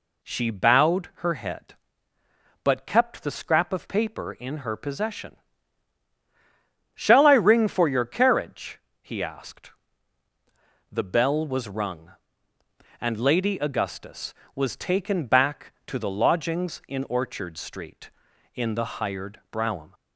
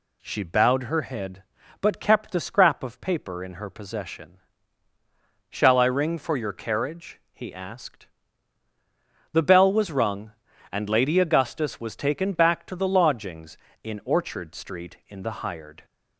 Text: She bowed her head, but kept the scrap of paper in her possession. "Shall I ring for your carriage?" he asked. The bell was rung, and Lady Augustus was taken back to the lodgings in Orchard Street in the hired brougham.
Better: first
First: none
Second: stops before "brougham"; at 15.8 s

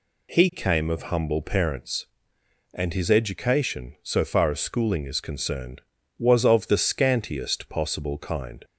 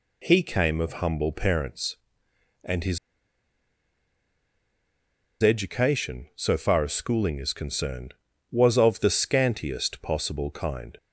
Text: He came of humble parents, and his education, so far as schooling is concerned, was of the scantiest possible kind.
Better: first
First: none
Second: pauses between "his" and "education"; strong; at 2.9 s; 2.4 s long

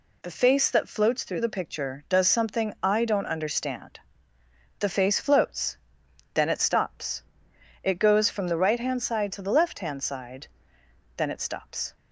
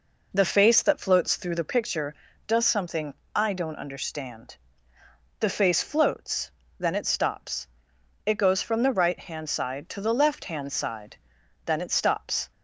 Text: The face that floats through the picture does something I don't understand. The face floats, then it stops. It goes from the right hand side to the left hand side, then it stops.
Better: first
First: none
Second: starts louder than the rest; noticeable; until 1.8 s; 4.5 dB // pauses between "something" and "I"; slight; at 3.1 s; 0.20 s long

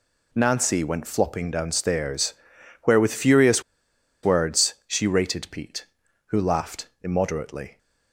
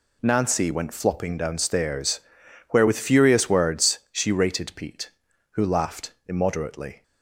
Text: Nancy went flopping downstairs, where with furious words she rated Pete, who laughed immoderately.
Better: second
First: pauses between "furious" and "words"; noticeable; at 3.6 s; 0.63 s long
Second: none

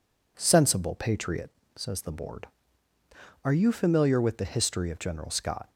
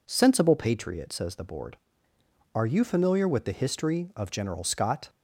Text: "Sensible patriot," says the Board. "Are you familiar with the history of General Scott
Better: neither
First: none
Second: none

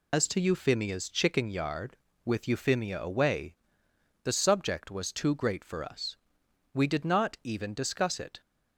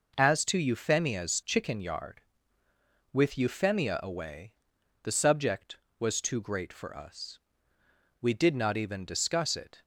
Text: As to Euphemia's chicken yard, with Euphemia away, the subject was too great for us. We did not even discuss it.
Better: second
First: loses the start of "As"; at 0.1 s; 130 ms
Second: none

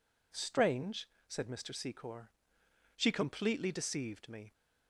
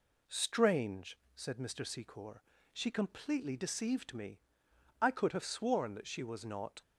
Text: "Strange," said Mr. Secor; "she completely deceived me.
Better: first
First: none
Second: goes on to say "I could have sworn that she was not"; strong; from 4.9 s on; 1.8 s long

